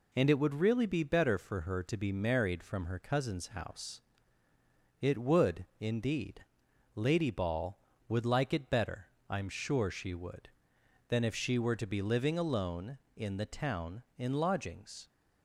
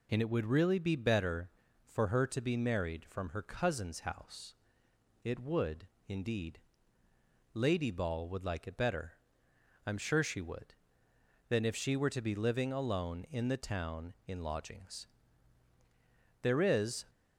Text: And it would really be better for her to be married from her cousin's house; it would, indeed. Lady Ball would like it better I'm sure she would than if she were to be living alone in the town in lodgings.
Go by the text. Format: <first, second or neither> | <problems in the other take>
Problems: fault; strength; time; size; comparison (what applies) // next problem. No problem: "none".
first | pauses between "better" and "I'm"; noticeable; at 9.1 s; 0.70 s long; slight in the first // goes on to say "There is"; noticeable; from 16.4 s on; 0.62 s long